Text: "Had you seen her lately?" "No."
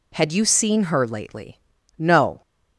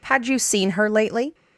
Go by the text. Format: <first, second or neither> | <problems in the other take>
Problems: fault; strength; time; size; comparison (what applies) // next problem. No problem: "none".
first | stops before "No"; at 1.3 s